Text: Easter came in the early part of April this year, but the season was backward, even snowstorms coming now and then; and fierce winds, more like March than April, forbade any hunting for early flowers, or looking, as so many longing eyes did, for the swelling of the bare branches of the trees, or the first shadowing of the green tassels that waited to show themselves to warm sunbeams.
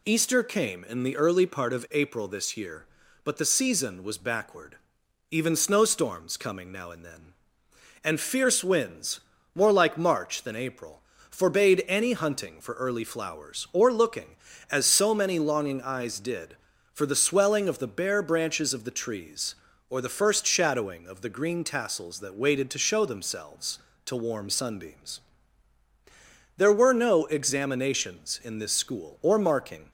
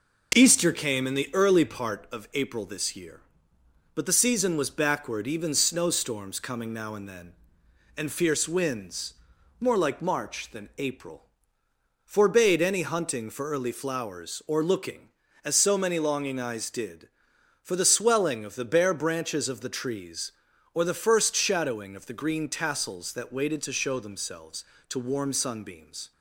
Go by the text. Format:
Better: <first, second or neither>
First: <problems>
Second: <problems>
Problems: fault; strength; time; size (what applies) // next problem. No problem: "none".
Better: second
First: goes on to say "There were no examinations in this school or marking"; strong; from 26.5 s on; 3.3 s long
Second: none